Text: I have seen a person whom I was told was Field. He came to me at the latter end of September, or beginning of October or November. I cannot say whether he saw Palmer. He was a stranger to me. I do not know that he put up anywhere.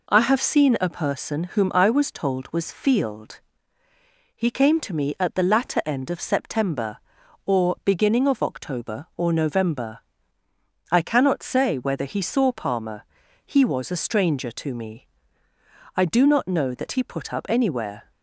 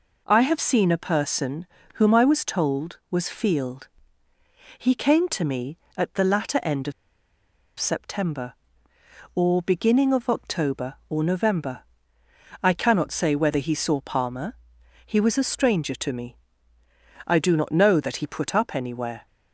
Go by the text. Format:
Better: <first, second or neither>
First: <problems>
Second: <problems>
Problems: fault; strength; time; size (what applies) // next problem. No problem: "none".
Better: first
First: none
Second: pauses between "person" and "whom"; slight; at 1.6 s; 0.30 s long // pauses between "of" and "September"; noticeable; at 6.9 s; 0.87 s long